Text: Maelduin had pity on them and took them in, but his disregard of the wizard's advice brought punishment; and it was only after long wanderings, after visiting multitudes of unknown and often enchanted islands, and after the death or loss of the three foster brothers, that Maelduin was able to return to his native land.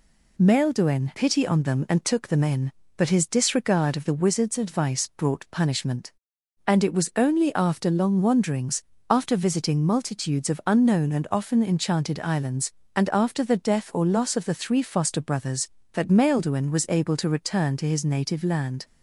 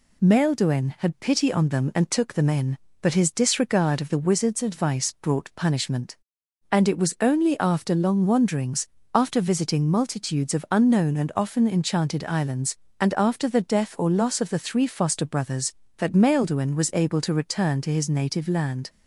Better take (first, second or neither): second